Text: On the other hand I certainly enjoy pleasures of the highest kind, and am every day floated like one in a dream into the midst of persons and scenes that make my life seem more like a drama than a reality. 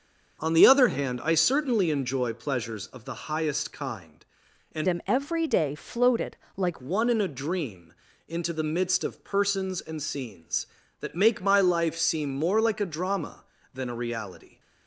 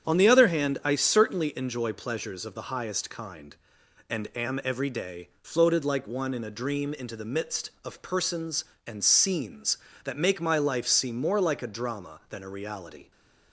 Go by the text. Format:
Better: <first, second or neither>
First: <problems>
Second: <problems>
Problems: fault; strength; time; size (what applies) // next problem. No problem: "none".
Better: second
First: starts louder than the rest; until 1.4 s; 6.5 dB // changes voice from "am" to "like"; from 4.8 to 6.8 s; 2.0 s long // pauses between "floated" and "like"; slight; at 6.3 s; 0.18 s long // pauses between "dream" and "into"; slight; at 7.9 s; 0.34 s long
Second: starts louder than the rest; strong; until 1.1 s; 8 dB